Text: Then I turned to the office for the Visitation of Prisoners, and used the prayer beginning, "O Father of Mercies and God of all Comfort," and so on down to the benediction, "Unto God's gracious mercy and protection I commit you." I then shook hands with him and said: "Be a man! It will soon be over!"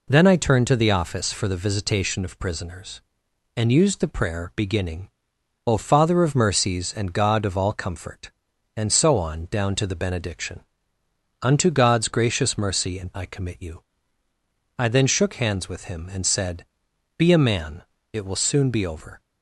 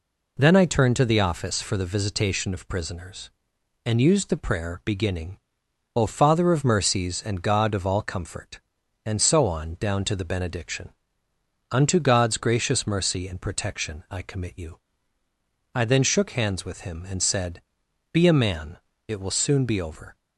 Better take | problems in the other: second | skips "protection"; at 13.1 s

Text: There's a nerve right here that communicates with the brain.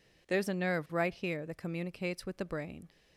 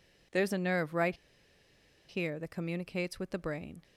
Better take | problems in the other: first | pauses between "right" and "here"; noticeable; at 1.1 s; 0.93 s long

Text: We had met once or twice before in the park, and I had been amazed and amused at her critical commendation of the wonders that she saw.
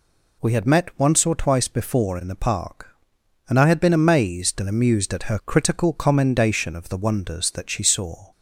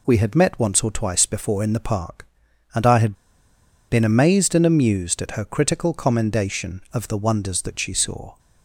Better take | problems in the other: first | pauses between "had" and "been"; noticeable; at 3.1 s; 0.74 s long

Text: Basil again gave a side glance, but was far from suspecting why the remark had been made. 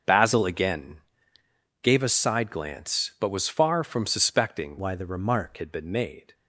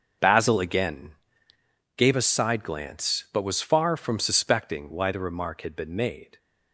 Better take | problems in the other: second | starts louder than the rest; until 1.9 s; 6.5 dB; also in the second // pauses between "again" and "gave"; noticeable; at 0.9 s; 0.84 s long; noticeable in the second // changes voice from "why" to "remark"; from 4.7 to 5.5 s; 0.8 s long

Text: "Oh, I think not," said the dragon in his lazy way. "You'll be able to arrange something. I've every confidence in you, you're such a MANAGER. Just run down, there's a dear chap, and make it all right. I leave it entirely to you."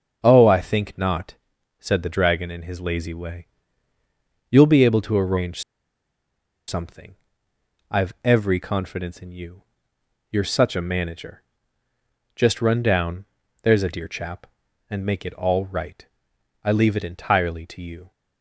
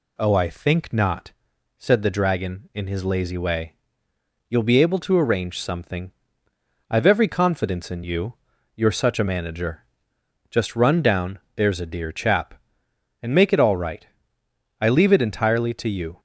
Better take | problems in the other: second | starts louder than the rest; until 1.2 s; 6.5 dB // pauses between "arrange" and "something"; at 5.6 s; 1.0 s long

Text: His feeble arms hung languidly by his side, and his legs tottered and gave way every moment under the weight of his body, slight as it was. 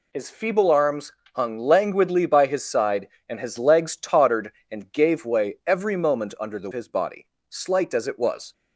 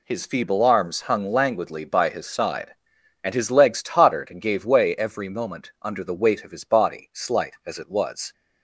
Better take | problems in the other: second | pauses between "arms" and "hung"; slight; at 1.1 s; 0.24 s long // skips "weight of"; at 6.7 s

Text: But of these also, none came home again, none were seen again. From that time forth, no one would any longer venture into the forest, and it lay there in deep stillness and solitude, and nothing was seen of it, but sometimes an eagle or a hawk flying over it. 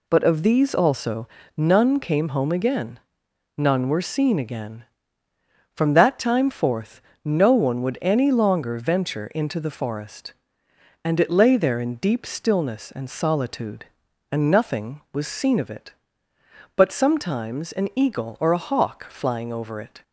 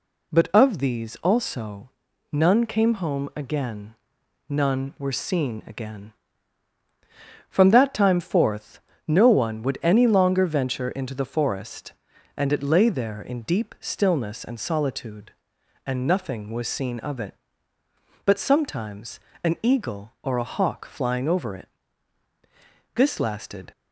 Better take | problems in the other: first | pauses between "sometimes" and "an"; slight; at 19.2 s; 0.24 s long // goes on to say "This lasted"; noticeable; from 22.9 s on; 0.76 s long

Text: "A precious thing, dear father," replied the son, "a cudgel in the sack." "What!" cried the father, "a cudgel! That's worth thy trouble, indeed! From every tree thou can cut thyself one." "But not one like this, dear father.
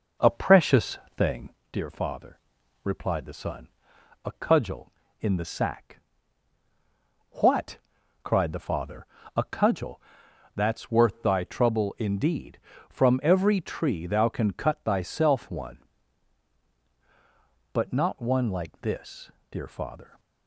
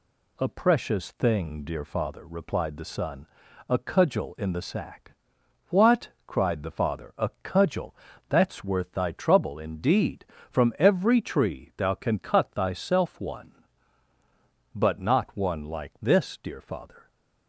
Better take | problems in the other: second | starts louder than the rest; noticeable; until 1.7 s; 5.5 dB // pauses between "precious" and "thing"; slight; at 0.9 s; 0.20 s long

